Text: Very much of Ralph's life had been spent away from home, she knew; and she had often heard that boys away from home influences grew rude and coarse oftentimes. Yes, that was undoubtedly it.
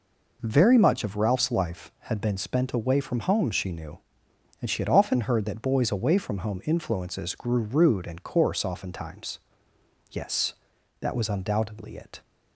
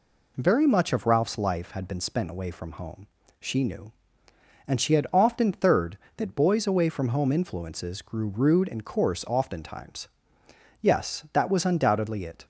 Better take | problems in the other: first | says "third" for "heard"; at 5.5 s

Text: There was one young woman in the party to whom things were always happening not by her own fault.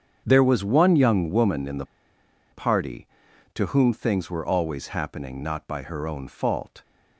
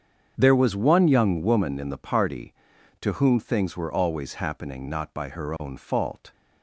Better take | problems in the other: second | starts louder than the rest; strong; until 1.2 s; 7.5 dB; strong in the second // pauses between "the" and "party"; noticeable; at 1.8 s; 0.67 s long

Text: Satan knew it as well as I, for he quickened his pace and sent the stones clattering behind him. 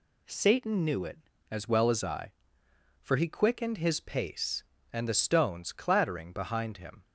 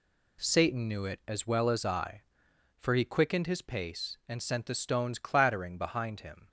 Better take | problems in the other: second | skips "sent"; at 5.0 s

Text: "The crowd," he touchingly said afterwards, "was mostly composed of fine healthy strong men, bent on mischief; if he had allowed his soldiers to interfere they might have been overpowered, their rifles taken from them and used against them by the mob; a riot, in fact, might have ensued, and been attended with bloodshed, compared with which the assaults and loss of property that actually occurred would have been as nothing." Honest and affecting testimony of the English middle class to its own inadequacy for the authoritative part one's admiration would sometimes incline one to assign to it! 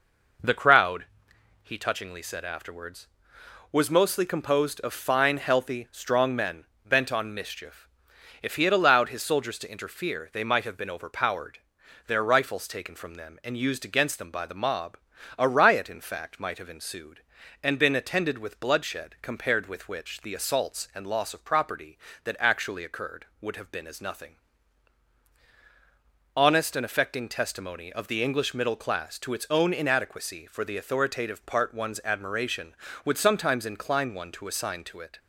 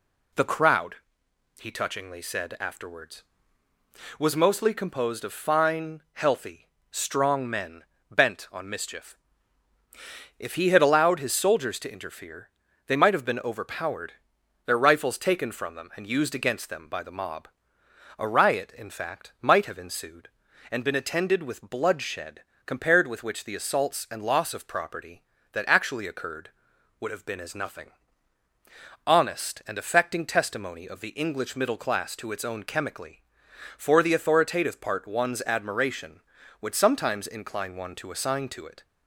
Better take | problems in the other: first | pauses between "healthy" and "strong"; slight; at 6.6 s; 0.24 s long // pauses between "interfere" and "they"; at 12.4 s; 0.38 s long // says "chemically" for "inadequacy"; at 32.6 s

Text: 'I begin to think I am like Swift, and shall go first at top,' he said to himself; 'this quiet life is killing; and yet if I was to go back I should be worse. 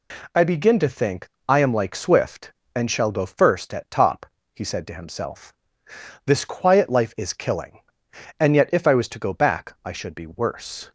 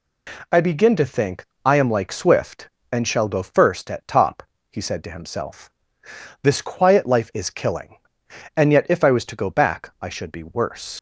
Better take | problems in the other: first | pauses between "think" and "I"; slight; at 1.4 s; 0.18 s long; slight in the first // leaves "worse" unfinished; at 10.9 s; 90 ms

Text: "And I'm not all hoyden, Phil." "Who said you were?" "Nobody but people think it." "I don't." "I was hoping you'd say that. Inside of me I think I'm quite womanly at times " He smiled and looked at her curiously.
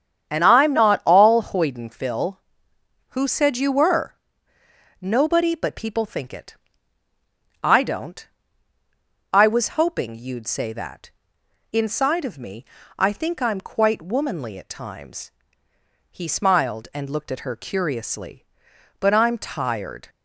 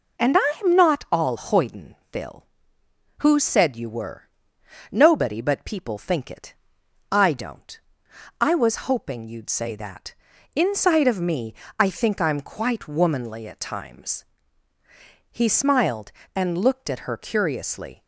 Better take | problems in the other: second | starts louder than the rest; strong; until 1.3 s; 8.5 dB // pauses between "me" and "I"; slight; at 12.6 s; 0.32 s long; slight in the second // goes on to say "But I'm tired"; noticeable; from 18.9 s on; 1.1 s long

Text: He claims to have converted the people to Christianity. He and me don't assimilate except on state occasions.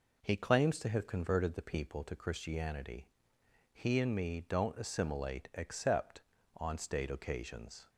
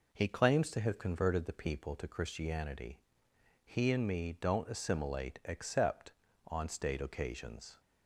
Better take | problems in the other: neither | none

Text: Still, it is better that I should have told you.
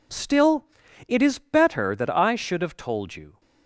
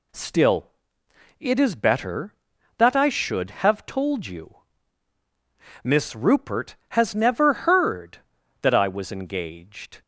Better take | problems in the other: first | goes on to say "Miss Rupert has never heard that I was engaged"; strong; from 5.8 s on; 4.1 s long

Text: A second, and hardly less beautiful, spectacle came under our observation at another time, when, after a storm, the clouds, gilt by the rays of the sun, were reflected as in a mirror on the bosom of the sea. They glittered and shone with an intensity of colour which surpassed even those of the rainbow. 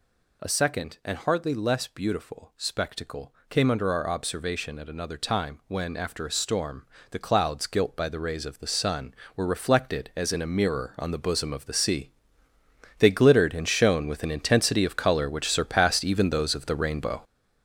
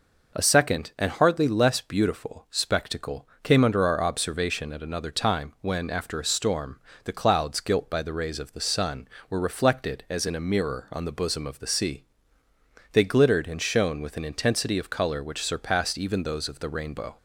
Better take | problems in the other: second | gets louder; strong; throughout; 8.5 dB // pauses between "spectacle" and "came"; slight; at 3.3 s; 0.16 s long; slight in the second

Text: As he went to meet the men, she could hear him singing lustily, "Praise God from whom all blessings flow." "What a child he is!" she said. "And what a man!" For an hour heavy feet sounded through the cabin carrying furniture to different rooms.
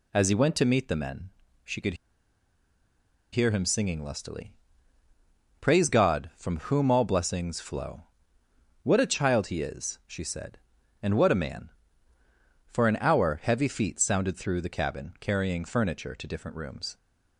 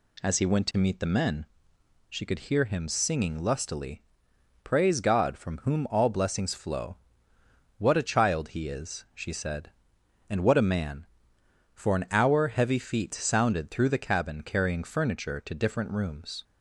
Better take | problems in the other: second | pauses between "could" and "hear"; strong; at 1.9 s; 1.3 s long

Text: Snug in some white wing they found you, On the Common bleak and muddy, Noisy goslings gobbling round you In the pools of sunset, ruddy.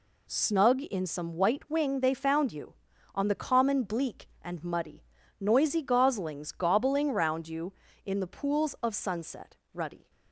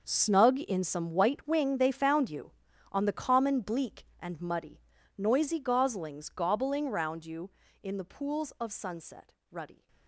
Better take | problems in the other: first | gets quieter; strong; throughout; 15 dB

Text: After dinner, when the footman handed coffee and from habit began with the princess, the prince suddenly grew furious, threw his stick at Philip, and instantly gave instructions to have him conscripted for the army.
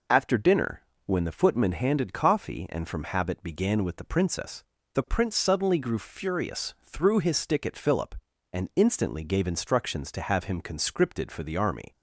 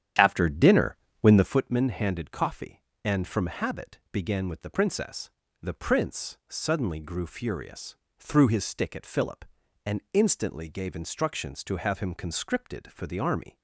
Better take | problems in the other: first | starts louder than the rest; strong; until 1.6 s; 10 dB

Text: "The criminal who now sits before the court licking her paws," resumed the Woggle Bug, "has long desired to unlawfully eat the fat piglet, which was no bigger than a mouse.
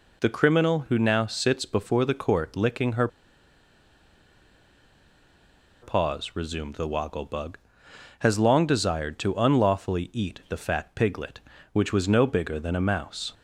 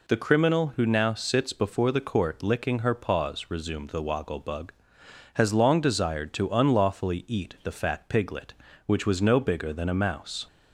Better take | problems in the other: second | pauses between "her" and "paws"; strong; at 3.0 s; 2.7 s long

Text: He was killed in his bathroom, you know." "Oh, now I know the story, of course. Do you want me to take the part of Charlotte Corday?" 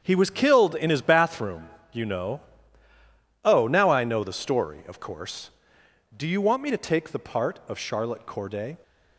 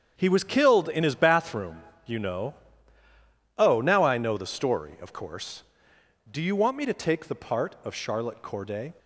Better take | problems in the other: neither | starts louder than the rest; strong; the same in both

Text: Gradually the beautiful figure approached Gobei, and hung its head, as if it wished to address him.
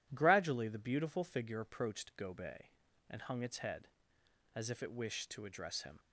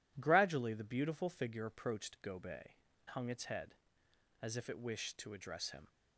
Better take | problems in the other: first | skips "and"; at 2.9 s

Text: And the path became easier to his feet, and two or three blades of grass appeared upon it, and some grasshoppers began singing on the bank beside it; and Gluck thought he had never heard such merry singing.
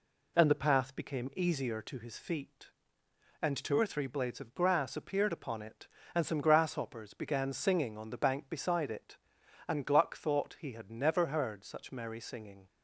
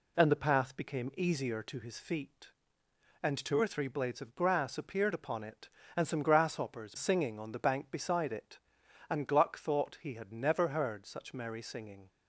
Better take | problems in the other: first | skips "began"; at 6.9 s

